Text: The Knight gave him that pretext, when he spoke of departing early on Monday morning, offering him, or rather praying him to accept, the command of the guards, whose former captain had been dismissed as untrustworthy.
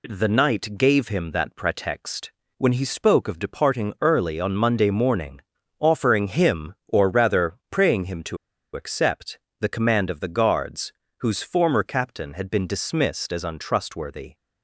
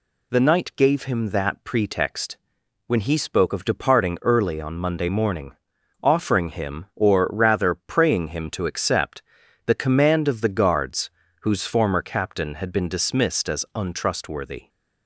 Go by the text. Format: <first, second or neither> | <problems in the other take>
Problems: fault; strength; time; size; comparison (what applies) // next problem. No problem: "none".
second | pauses between "rather" and "praying"; slight; at 7.5 s; 0.16 s long // pauses between "to" and "accept"; at 8.3 s; 0.37 s long